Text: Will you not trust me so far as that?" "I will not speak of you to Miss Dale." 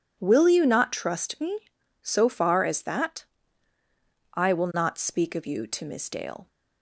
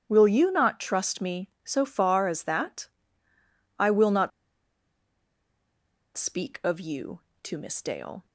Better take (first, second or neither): first